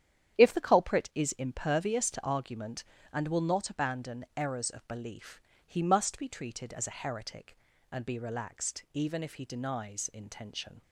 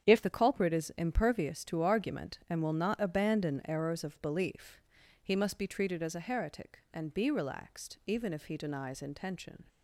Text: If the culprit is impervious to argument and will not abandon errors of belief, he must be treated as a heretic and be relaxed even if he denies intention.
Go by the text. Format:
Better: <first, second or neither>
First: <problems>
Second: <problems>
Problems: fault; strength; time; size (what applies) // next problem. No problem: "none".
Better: first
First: starts louder than the rest; strong; until 1.4 s; 9.5 dB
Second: starts louder than the rest; strong; until 1.1 s; 8.5 dB // changes voice at "the"; from 0.2 s on; 9.4 s long